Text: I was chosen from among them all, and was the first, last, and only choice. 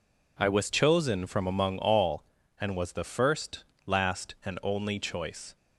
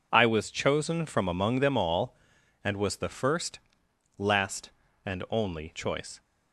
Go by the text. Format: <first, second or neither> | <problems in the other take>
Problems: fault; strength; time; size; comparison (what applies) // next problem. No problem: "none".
second | skips "them"; at 1.7 s